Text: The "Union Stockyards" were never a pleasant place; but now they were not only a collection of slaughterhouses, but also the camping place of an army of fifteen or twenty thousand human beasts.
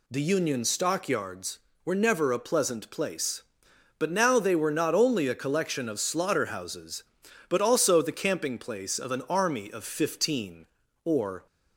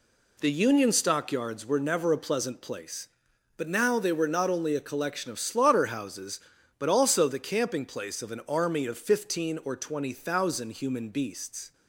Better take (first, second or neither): second